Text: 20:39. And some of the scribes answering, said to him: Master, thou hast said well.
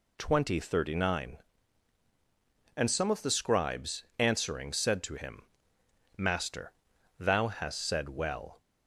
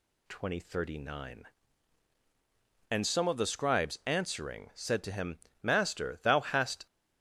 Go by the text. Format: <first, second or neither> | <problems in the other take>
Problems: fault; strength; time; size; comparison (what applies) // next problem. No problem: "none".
first | stops before "said well"; at 6.8 s